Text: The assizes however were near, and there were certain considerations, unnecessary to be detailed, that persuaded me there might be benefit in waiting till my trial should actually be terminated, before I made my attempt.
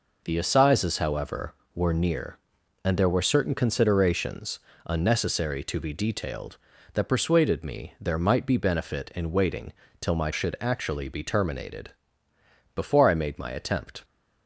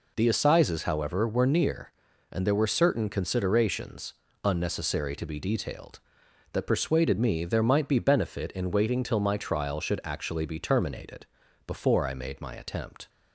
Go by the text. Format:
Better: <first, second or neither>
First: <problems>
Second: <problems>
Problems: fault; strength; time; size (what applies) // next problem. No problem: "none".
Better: second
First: pauses between "waiting" and "till"; slight; at 9.7 s; 0.26 s long // skips "trial"; at 10.3 s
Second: none